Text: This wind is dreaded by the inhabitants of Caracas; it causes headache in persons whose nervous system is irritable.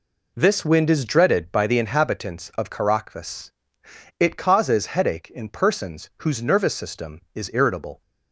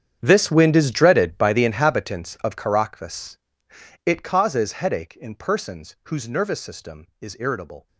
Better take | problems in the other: first | gets quieter; strong; throughout; 17.5 dB

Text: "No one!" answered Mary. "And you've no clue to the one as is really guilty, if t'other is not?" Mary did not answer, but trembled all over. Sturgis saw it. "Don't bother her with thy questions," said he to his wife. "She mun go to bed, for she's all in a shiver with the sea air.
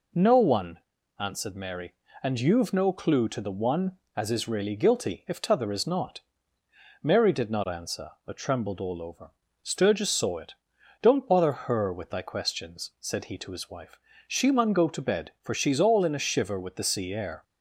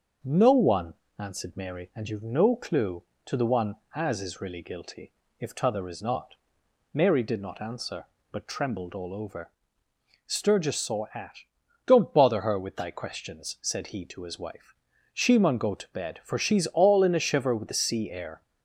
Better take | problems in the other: first | starts louder than the rest; until 1.4 s; 6 dB // says "at" for "it"; at 11.1 s

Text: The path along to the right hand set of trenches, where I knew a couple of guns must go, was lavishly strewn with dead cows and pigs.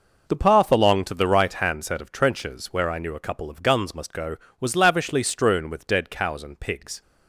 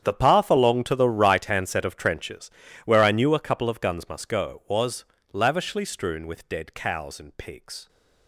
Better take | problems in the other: first | gets quieter; strong; throughout; 17 dB // pauses between "was" and "lavishly"; slight; at 5.0 s; 0.26 s long

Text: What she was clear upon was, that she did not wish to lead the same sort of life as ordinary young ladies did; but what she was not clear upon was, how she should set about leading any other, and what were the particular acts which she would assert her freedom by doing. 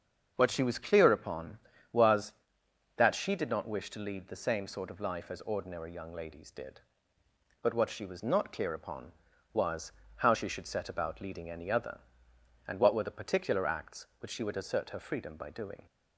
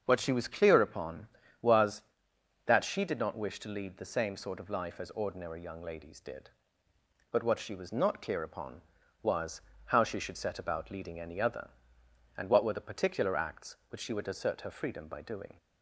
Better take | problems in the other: neither | starts louder than the rest; the same in both

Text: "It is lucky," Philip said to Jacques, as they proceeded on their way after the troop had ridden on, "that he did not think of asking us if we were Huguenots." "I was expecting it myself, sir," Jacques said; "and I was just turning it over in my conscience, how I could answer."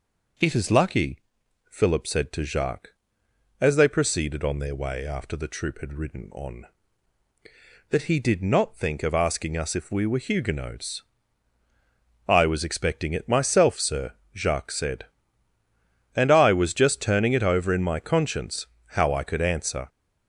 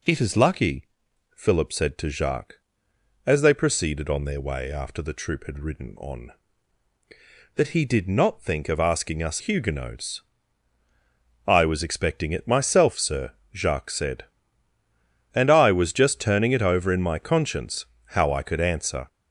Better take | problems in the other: first | skips "if we were"; at 9.3 s

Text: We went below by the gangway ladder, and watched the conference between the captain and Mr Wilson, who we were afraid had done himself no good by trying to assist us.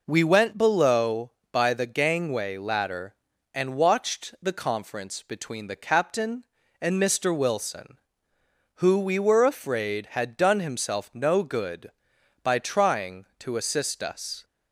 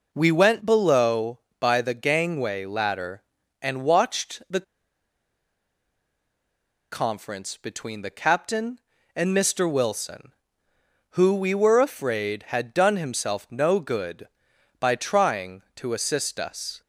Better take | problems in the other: first | pauses between "the" and "conference"; strong; at 4.6 s; 2.2 s long

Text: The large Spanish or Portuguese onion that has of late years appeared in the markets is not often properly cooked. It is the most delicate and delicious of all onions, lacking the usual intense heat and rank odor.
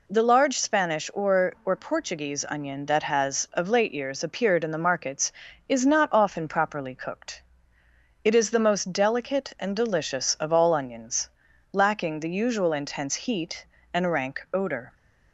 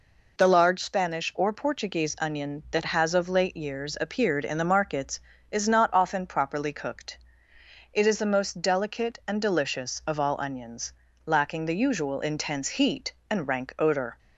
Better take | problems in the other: second | says "or" twice; at 1.6 s

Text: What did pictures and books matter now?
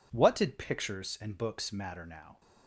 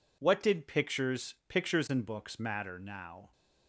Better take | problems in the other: first | says "pictures" twice; at 1.4 s

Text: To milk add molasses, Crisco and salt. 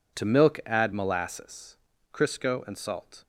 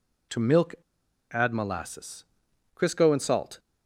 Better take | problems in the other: first | pauses between "milk" and "add"; noticeable; at 0.7 s; 0.56 s long

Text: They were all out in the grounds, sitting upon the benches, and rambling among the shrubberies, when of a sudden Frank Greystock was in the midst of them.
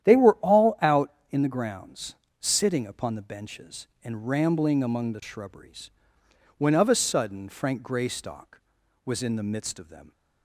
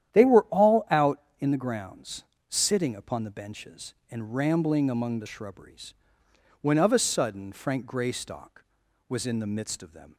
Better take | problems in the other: neither | starts louder than the rest; strong; the same in both

